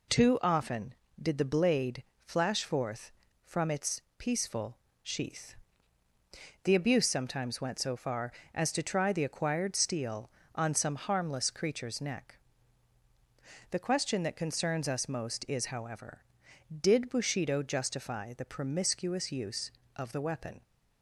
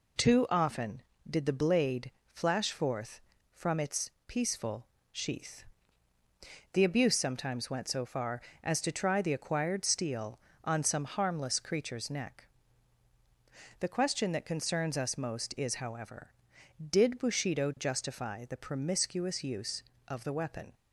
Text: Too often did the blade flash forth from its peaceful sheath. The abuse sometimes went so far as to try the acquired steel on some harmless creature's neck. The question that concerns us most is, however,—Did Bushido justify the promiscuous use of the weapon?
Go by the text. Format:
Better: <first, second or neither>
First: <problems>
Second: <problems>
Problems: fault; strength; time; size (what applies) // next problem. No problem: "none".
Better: neither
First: pauses between "blade" and "flash"; slight; at 2.0 s; 0.22 s long // pauses between "its" and "peaceful"; slight; at 3.9 s; 0.18 s long // pauses between "peaceful" and "sheath"; slight; at 4.7 s; 0.24 s long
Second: pauses between "blade" and "flash"; slight; at 2.1 s; 0.22 s long // pauses between "its" and "peaceful"; slight; at 4.0 s; 0.18 s long // pauses between "peaceful" and "sheath"; slight; at 4.8 s; 0.24 s long